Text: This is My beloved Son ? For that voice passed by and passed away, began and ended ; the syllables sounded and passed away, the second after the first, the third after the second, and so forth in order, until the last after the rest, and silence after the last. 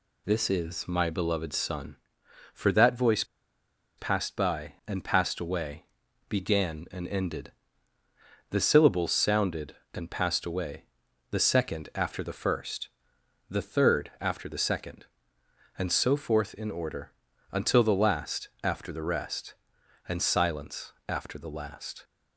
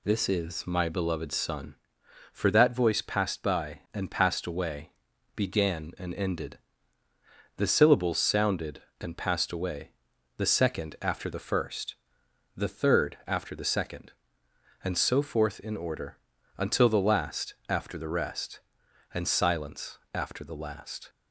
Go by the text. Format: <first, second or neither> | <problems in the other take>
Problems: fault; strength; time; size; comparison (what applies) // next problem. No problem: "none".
second | pauses between "voice" and "passed"; noticeable; at 3.2 s; 0.73 s long // pauses between "silence" and "after"; slight; at 20.9 s; 0.16 s long; slight in the second